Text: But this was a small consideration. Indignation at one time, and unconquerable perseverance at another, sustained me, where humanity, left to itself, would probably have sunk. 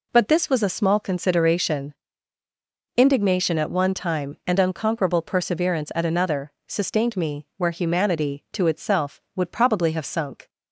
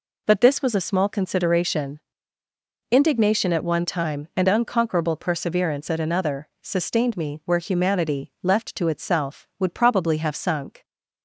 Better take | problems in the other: second | skips "left"; at 8.4 s

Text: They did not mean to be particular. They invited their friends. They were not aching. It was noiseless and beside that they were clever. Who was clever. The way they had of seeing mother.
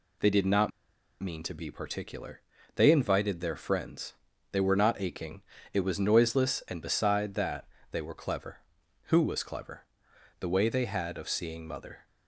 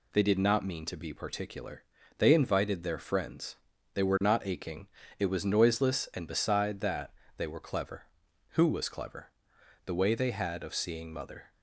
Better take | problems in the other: second | pauses between "not" and "mean"; noticeable; at 0.7 s; 0.51 s long // pauses between "that" and "they"; slight; at 7.6 s; 0.26 s long; slight in the second

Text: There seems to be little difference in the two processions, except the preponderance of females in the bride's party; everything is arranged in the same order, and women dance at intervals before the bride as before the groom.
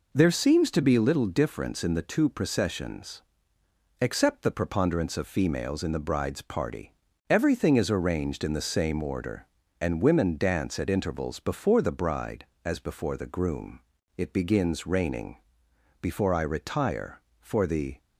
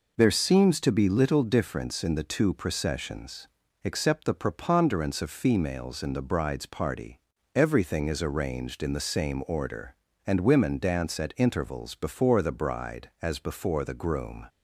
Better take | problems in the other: second | goes on to say "It begins raining before I retire for the"; strong; from 14.1 s on; 3.8 s long

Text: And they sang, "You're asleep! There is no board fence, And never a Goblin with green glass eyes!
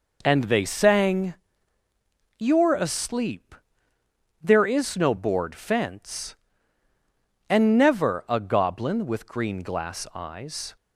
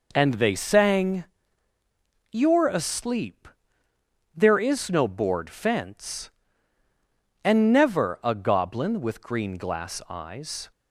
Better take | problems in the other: neither | none

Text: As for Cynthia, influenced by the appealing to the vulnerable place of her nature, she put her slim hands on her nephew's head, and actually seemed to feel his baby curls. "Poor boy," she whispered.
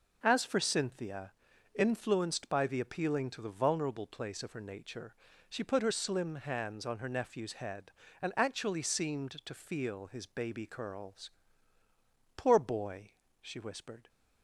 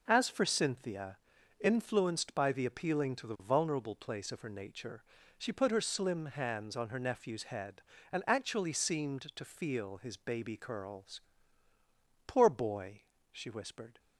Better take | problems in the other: neither | none

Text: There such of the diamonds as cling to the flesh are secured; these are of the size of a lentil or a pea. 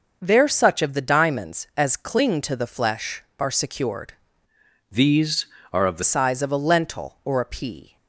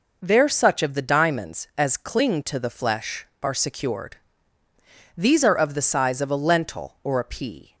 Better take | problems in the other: second | changes voice from "these" to "the"; from 4.8 to 6.0 s; 1.2 s long

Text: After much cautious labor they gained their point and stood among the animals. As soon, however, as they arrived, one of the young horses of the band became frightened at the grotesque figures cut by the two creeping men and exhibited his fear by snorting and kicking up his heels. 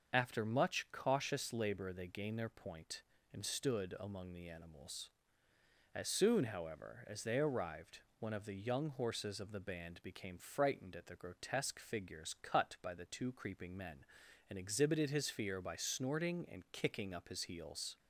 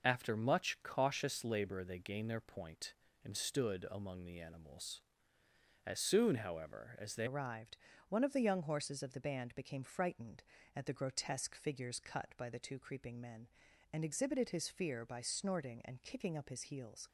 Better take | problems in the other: first | starts louder than the rest; noticeable; until 1.0 s; 6 dB; also in the first // changes voice at "arrived"; from 7.2 s on; 9.8 s long

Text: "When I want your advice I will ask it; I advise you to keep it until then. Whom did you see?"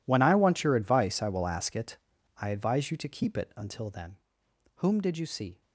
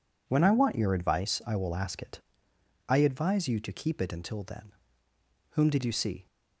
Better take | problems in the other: second | gets quieter; strong; throughout; 17.5 dB

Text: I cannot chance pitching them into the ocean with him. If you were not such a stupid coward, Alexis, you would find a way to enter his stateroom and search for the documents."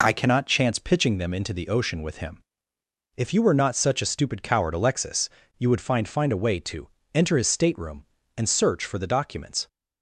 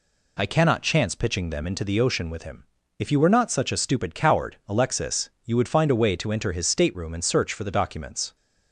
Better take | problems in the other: second | says "find" twice; at 6.0 s // pauses between "to" and "enter"; slight; at 6.8 s; 0.24 s long

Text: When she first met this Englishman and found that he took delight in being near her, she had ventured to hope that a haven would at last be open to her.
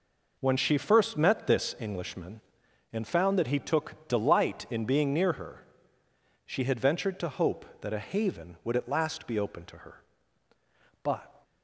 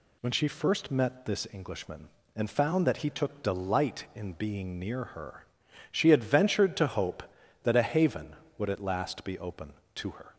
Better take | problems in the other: second | goes on to say "But"; slight; from 11.0 s on; 0.40 s long

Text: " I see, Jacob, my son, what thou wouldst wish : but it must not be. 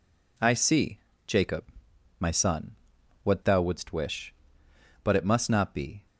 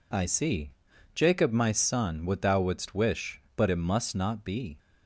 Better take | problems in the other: neither | none

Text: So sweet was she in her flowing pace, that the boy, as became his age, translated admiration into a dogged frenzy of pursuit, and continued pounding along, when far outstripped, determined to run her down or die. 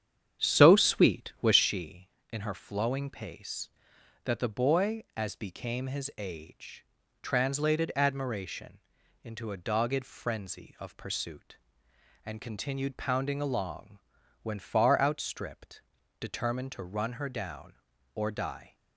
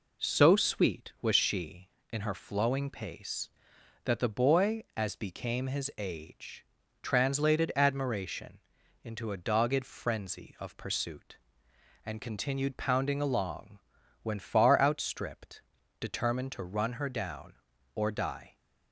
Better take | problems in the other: second | starts louder than the rest; strong; until 1.7 s; 9 dB // pauses between "admiration" and "into"; at 8.7 s; 0.44 s long; also in the second

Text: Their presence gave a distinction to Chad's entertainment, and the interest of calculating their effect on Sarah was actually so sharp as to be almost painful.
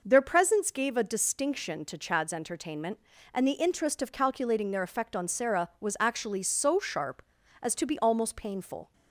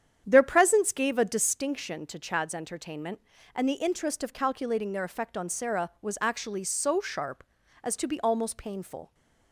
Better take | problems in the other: first | starts louder than the rest; strong; until 1.7 s; 9 dB

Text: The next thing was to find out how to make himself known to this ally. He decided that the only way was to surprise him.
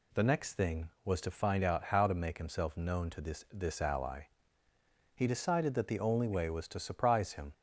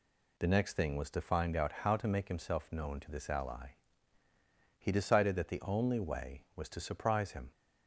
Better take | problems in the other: second | says "this" twice; at 3.5 s

